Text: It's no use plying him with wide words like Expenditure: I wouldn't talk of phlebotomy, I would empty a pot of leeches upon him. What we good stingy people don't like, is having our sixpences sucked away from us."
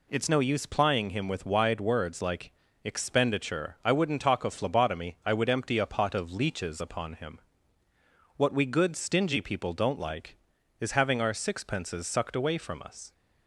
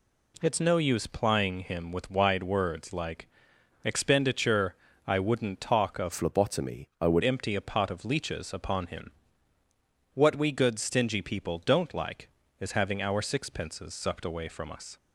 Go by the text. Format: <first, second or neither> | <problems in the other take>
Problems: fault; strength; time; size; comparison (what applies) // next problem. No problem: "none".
first | pauses between "like" and "Expenditure"; noticeable; at 3.2 s; 0.58 s long; slight in the first // changes voice from "phlebotomy" to "would"; from 6.1 to 7.2 s; 1.1 s long